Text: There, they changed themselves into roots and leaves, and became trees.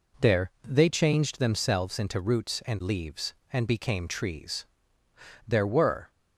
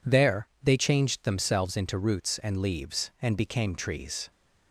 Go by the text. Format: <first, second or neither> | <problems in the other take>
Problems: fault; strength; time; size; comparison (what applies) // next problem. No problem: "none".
second | goes on to say "There were"; noticeable; from 5.4 s on; 0.64 s long